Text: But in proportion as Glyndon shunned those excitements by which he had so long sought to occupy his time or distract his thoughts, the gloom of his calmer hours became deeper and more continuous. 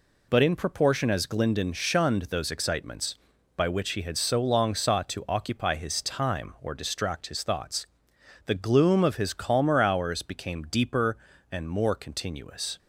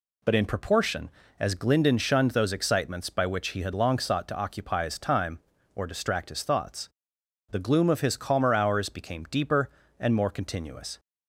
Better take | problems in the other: first | skips "so"; at 3.7 s

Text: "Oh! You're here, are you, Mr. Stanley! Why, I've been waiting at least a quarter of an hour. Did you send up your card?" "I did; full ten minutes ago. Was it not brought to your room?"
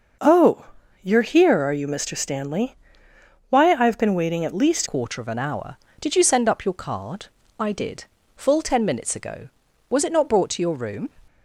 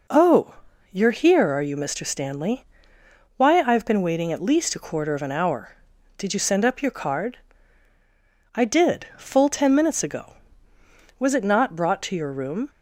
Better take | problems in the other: second | changes voice at "a"; from 4.8 s on; 6.2 s long

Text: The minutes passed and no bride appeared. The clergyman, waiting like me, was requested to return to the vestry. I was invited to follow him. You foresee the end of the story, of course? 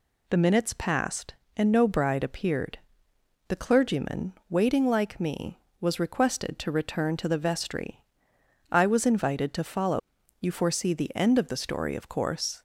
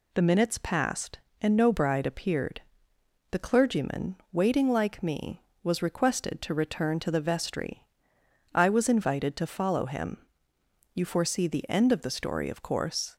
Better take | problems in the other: second | skips "him"; at 10.2 s

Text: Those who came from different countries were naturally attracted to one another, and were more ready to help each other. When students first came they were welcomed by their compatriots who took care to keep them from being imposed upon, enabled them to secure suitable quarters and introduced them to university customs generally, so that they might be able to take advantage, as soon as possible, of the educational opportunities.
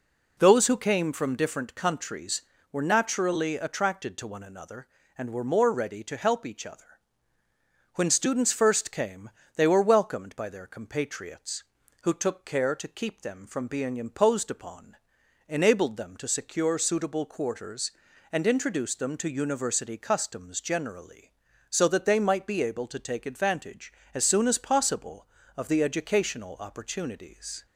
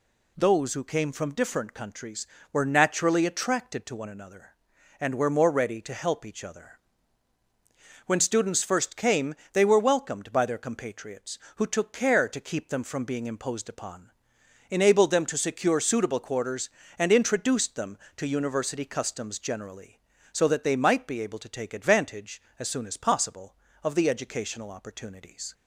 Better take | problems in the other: neither | pauses between "came" and "they"; slight; the same in both

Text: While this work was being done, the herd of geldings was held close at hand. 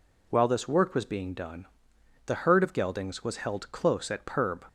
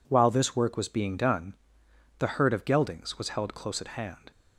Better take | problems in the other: second | says "perb" for "hand"; at 4.2 s

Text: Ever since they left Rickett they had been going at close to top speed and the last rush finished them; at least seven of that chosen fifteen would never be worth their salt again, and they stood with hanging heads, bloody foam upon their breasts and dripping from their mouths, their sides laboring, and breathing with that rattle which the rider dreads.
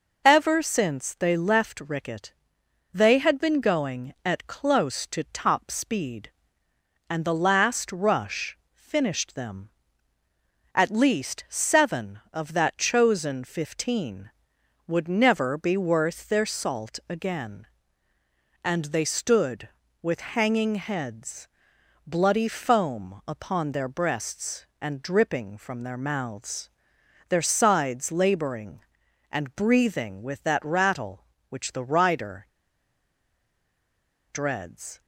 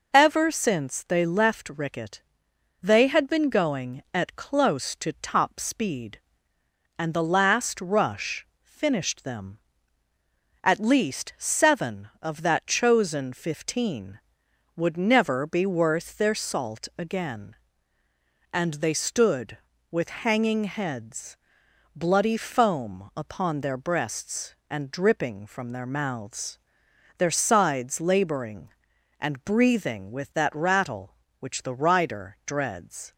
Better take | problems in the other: second | pauses between "Rickett" and "they"; noticeable; at 2.3 s; 0.60 s long; noticeable in the second // pauses between "rush" and "finished"; slight; at 8.5 s; 0.16 s long; slight in the second // pauses between "rider" and "dreads"; strong; at 32.4 s; 1.8 s long

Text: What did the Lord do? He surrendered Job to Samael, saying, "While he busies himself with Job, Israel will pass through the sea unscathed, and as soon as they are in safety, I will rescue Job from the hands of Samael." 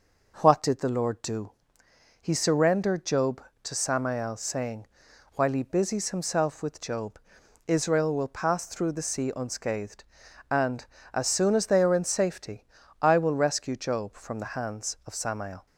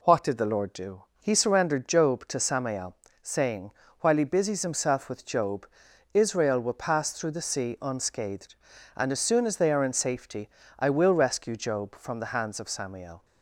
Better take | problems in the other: neither | none

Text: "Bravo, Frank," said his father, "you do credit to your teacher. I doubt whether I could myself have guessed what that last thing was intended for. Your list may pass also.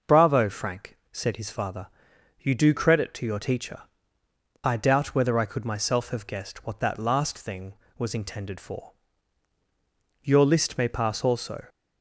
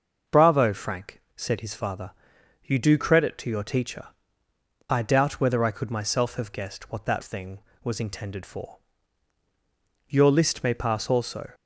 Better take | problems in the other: first | skips "last"; at 7.2 s

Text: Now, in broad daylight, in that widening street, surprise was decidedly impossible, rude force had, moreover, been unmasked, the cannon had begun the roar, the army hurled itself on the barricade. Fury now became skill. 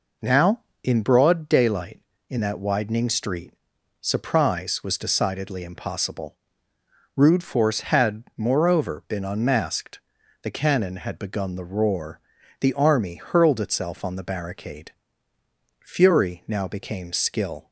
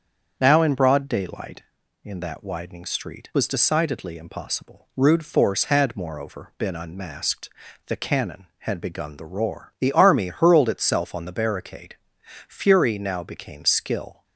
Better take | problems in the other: first | starts louder than the rest; strong; until 1.3 s; 7 dB // skips "surprise"; at 3.3 s

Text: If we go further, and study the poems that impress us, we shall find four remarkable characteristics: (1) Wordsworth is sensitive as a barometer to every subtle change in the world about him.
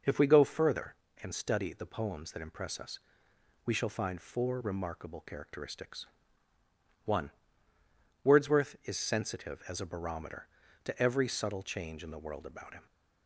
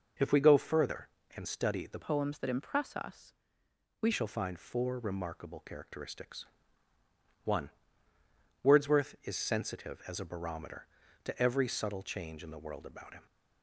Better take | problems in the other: first | changes voice from "poems" to "we"; from 2.0 to 4.0 s; 2.0 s long

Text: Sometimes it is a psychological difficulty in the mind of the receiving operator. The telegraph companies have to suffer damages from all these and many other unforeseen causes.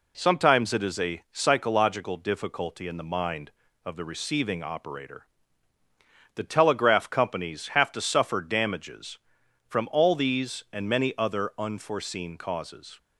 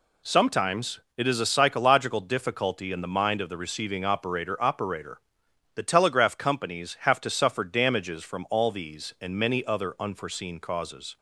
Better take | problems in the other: first | pauses between "Sometimes" and "it"; slight; at 1.0 s; 0.16 s long // says "operator" twice; at 4.6 s

